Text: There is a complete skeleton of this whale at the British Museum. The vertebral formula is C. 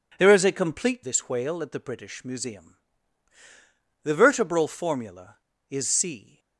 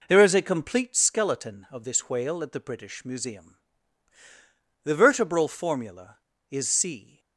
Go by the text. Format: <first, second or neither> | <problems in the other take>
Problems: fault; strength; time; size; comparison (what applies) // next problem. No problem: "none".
second | skips "skeleton of"; at 1.0 s